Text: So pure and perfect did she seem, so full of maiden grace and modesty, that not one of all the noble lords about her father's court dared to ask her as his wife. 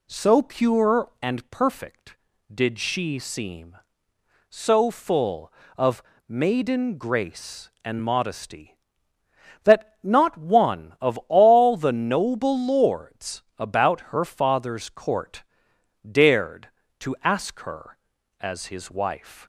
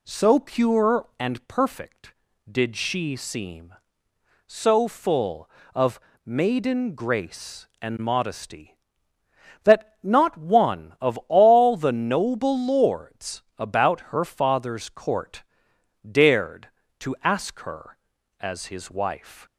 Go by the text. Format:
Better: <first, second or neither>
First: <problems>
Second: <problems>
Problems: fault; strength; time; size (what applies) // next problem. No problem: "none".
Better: neither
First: pauses between "of" and "maiden"; slight; at 6.0 s; 0.26 s long // pauses between "lords" and "about"; slight; at 13.4 s; 0.16 s long // pauses between "about" and "her"; slight; at 13.9 s; 0.16 s long // pauses between "court" and "dared"; noticeable; at 15.4 s; 0.66 s long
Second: pauses between "of" and "maiden"; slight; at 5.9 s; 0.26 s long // pauses between "lords" and "about"; slight; at 13.4 s; 0.16 s long // pauses between "about" and "her"; slight; at 13.9 s; 0.16 s long // pauses between "court" and "dared"; noticeable; at 15.4 s; 0.66 s long